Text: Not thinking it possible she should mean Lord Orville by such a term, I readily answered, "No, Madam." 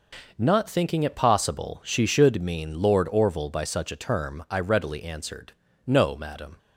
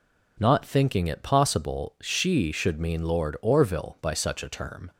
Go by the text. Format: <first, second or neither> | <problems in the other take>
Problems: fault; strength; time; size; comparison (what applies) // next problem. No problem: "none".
first | stops before "I readily answered No Madam"; at 4.9 s